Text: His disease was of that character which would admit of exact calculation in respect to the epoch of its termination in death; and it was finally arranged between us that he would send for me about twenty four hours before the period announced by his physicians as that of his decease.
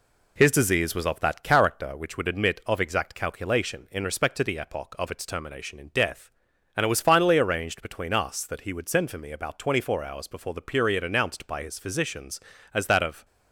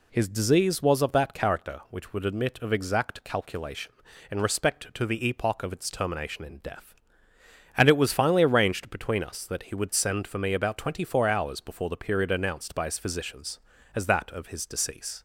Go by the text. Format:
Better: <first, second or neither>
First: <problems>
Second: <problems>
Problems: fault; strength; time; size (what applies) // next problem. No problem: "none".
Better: second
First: stops before "his decease"; at 13.2 s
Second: none